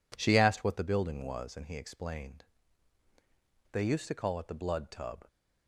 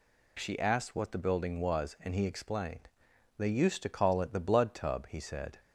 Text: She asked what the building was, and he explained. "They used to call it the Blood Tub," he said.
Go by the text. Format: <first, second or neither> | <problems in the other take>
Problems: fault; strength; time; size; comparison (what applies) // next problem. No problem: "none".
second | stops before "he said"; at 5.2 s